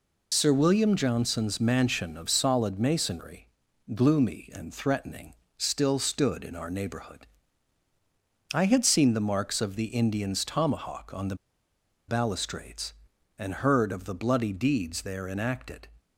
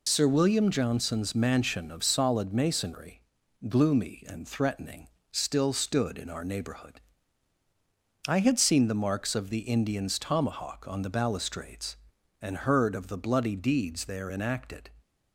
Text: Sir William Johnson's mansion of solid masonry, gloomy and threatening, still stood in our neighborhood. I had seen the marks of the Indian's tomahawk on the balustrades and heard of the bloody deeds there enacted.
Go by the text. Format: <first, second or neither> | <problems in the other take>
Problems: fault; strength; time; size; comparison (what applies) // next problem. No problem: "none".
second | pauses between "the" and "balustrades"; noticeable; at 11.3 s; 0.73 s long